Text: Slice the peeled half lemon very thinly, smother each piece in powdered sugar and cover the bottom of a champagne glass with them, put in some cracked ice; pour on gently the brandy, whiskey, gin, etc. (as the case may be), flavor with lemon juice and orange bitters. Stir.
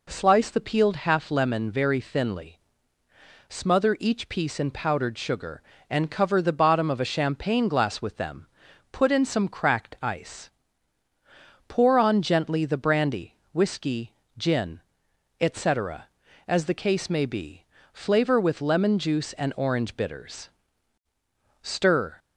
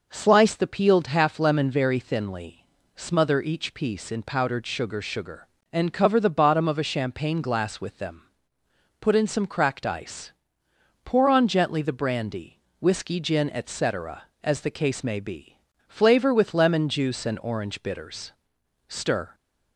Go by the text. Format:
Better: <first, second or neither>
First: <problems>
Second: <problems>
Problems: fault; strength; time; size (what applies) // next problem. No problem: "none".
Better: first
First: none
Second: says "sugar" twice; at 5.0 s